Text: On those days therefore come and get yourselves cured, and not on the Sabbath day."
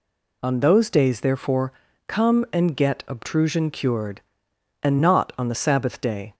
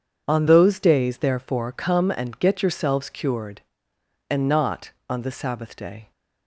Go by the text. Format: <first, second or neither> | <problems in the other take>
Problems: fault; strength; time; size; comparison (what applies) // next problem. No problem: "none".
second | pauses between "therefore" and "come"; slight; at 1.7 s; 0.34 s long // says "obtrusion" for "yourselves"; at 3.0 s